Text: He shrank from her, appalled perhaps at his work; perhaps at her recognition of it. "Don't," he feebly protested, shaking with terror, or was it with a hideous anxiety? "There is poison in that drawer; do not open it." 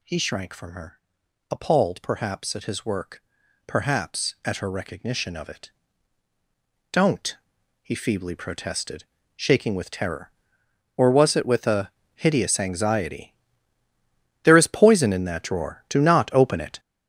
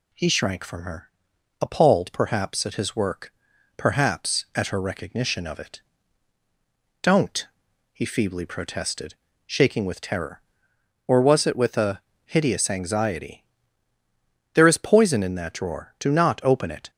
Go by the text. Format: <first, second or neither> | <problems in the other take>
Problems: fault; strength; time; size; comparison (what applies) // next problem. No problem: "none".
second | gets louder; strong; throughout; 8.5 dB // pauses between "a" and "hideous"; slight; at 11.9 s; 0.24 s long; slight in the second